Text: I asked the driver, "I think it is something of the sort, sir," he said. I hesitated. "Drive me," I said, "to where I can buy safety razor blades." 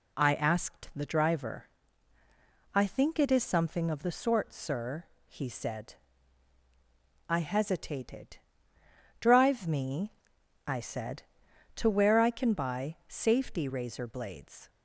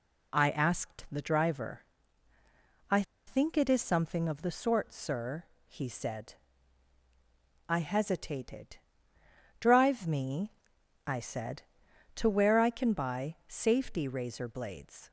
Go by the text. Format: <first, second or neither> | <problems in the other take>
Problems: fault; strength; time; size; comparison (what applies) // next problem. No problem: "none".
first | pauses between "I" and "think"; slight; at 3.0 s; 0.25 s long